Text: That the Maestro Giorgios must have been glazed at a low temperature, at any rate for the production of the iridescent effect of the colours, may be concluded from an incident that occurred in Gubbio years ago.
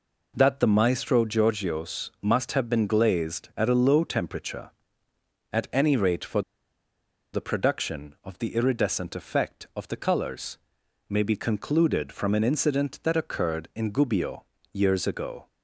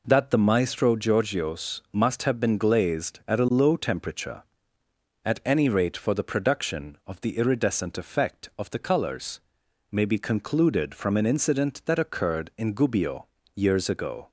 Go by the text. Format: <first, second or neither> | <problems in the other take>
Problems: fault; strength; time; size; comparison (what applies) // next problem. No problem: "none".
second | pauses between "for" and "the"; noticeable; at 6.4 s; 0.92 s long // pauses between "Gubbio" and "years"; slight; at 14.4 s; 0.28 s long; slight in the second